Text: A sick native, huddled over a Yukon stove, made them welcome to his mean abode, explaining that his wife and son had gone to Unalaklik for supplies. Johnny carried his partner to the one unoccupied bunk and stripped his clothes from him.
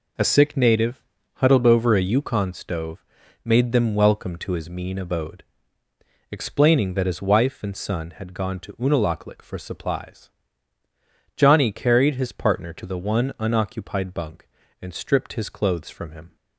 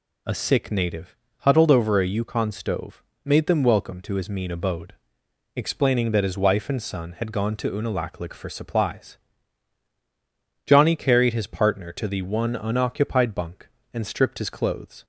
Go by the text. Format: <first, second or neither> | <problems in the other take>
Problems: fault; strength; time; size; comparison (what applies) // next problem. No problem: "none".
first | stops before "from him"; at 15.0 s